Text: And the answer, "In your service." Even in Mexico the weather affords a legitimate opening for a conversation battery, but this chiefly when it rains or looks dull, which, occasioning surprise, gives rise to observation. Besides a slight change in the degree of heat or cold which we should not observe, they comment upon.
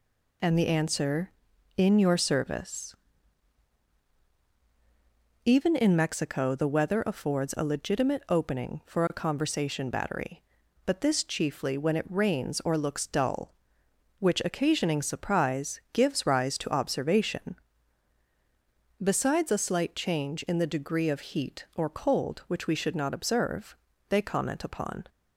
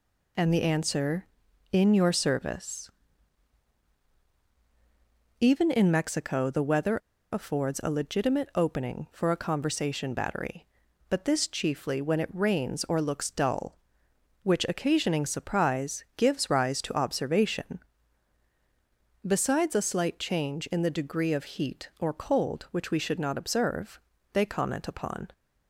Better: first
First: none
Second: pauses between "weather" and "affords"; slight; at 6.9 s; 0.35 s long

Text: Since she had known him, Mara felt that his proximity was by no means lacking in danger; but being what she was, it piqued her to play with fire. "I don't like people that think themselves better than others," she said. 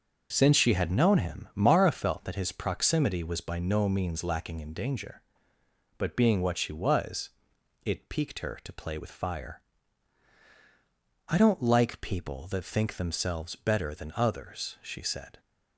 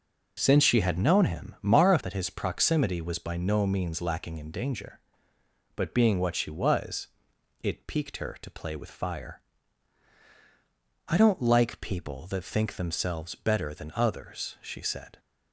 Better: first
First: none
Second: skips "felt"; at 1.9 s

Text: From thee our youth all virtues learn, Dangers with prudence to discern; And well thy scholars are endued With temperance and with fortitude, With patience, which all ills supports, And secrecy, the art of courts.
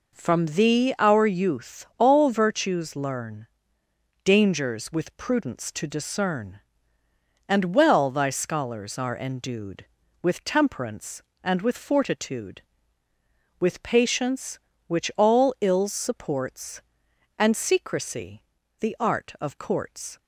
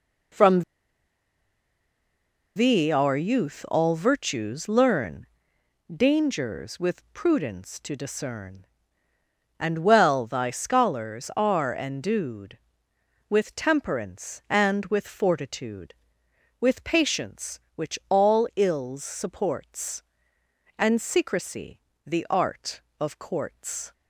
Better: first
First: none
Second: pauses between "From" and "thee"; strong; at 0.6 s; 1.9 s long

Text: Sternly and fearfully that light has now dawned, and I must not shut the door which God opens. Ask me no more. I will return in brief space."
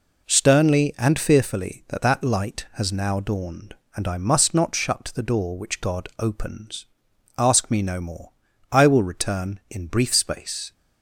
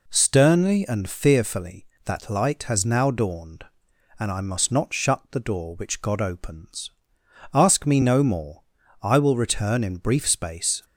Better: second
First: says "that" twice; at 2.0 s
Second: none

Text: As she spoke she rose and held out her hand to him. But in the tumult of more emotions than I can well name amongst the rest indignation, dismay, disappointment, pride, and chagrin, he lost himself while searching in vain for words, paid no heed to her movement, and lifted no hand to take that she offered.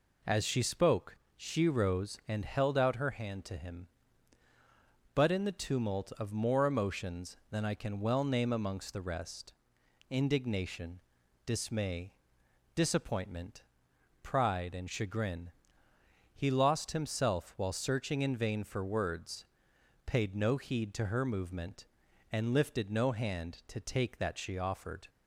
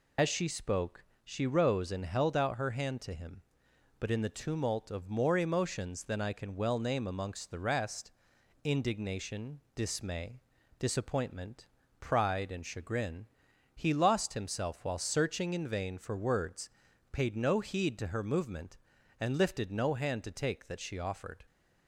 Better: first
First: pauses between "spoke" and "she"; slight; at 1.1 s; 0.20 s long // pauses between "rest" and "indignation"; noticeable; at 9.5 s; 0.56 s long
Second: loses the start of "As"; at 0.1 s; 65 ms // pauses between "spoke" and "she"; slight; at 1.0 s; 0.22 s long // pauses between "rest" and "indignation"; noticeable; at 8.1 s; 0.52 s long

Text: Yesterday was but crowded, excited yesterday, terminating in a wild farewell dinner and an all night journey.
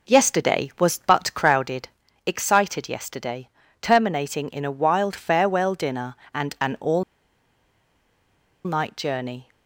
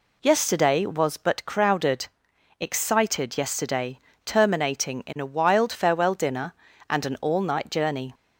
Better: second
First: pauses between "all" and "night"; strong; at 7.0 s; 1.6 s long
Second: none

